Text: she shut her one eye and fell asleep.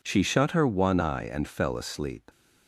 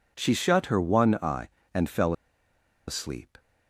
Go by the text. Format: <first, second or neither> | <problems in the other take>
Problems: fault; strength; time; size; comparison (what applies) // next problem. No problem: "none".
first | pauses between "fell" and "asleep"; noticeable; at 2.1 s; 0.75 s long